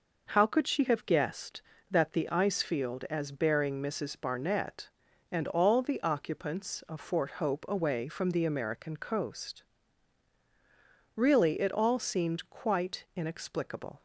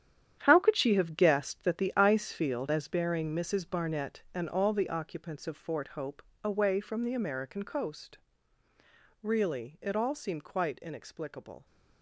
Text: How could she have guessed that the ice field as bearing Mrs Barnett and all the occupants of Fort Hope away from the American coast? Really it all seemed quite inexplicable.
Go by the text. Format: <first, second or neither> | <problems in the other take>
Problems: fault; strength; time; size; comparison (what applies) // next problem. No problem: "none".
first | gets quieter; strong; throughout; 11.5 dB // pauses between "Hope" and "away"; slight; at 6.2 s; 0.22 s long